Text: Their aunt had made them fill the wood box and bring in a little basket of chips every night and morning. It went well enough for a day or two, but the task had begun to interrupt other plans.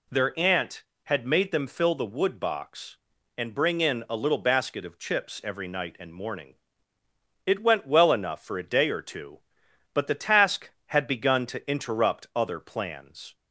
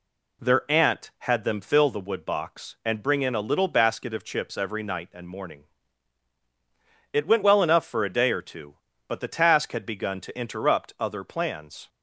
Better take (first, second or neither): first